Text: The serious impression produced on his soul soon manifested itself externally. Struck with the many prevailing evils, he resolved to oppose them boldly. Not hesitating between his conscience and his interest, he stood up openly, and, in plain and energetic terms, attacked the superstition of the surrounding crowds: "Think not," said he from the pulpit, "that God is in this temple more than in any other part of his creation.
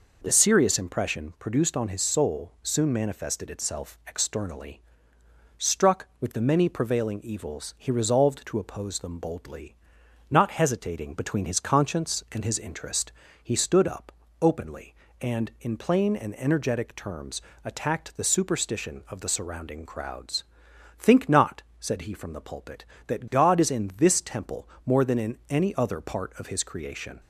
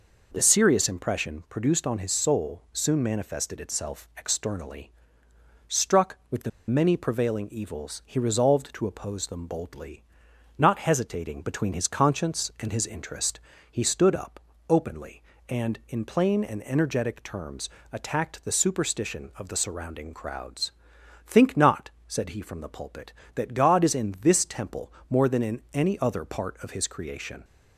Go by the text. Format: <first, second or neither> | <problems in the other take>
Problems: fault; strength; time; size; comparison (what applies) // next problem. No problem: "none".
first | pauses between "the" and "many"; slight; at 6.5 s; 0.17 s long // pauses between "up" and "openly"; slight; at 14.3 s; 0.28 s long; slight in the first // pauses between "temple" and "more"; slight; at 24.9 s; 0.16 s long; slight in the first